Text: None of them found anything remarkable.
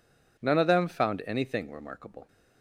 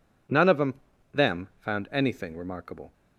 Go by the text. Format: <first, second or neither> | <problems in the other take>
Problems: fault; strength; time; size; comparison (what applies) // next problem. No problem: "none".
first | says "them" twice; at 1.1 s